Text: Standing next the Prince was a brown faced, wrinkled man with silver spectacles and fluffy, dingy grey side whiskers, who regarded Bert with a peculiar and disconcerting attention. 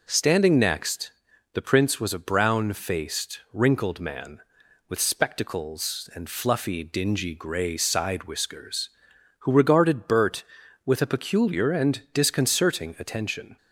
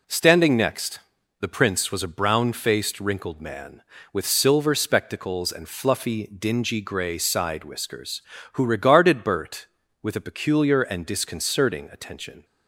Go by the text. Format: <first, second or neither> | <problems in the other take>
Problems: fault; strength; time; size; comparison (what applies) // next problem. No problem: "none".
second | pauses between "next" and "the"; at 1.1 s; 0.42 s long; also in the second // skips "silver"; at 5.0 s